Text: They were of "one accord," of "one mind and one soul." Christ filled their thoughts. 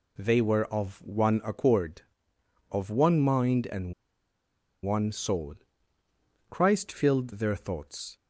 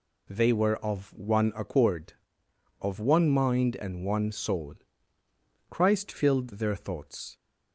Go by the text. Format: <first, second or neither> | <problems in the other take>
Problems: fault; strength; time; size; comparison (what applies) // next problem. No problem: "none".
second | pauses between "and" and "one"; noticeable; at 3.9 s; 0.91 s long